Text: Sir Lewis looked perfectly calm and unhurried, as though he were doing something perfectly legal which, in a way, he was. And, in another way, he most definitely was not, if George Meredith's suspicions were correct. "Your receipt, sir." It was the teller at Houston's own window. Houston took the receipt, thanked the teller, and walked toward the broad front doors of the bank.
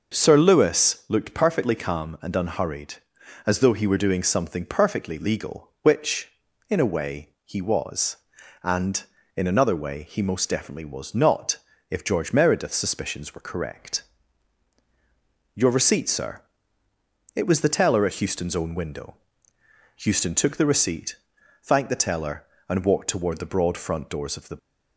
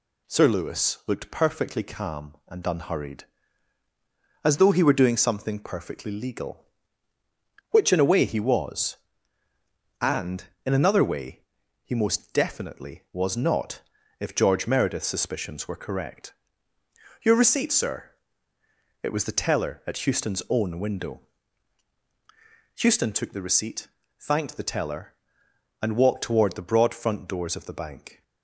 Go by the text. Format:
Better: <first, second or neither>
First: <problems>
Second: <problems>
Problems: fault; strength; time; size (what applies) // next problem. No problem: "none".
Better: second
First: stops before "bank"; at 24.5 s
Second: none